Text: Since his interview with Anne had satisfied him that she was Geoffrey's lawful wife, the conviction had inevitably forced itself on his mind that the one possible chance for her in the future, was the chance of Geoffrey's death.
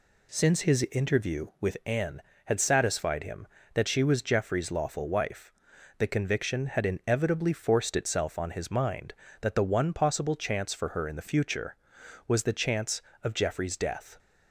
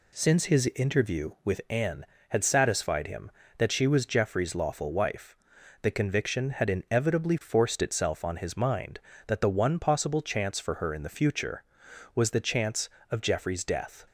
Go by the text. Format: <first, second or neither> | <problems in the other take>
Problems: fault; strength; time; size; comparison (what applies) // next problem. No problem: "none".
neither | none